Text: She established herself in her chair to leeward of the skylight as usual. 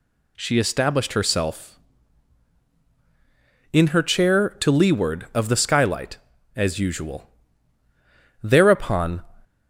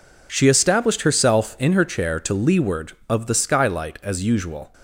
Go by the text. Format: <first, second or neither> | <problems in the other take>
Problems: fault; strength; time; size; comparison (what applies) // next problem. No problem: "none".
second | goes on to say "Thereupon"; noticeable; from 8.4 s on; 0.80 s long